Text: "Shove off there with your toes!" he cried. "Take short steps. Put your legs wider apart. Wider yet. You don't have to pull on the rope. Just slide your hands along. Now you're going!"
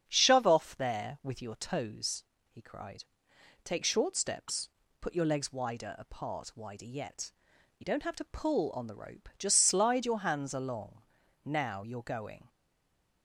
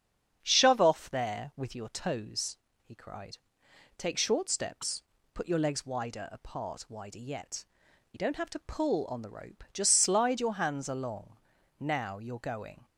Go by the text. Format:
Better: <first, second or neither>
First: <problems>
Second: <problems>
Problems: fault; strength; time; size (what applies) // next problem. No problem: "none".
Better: second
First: starts louder than the rest; strong; until 1.0 s; 8 dB // stays silent after the last word; slight; from 12.4 s on; 0.8 s long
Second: starts louder than the rest; strong; until 1.4 s; 8 dB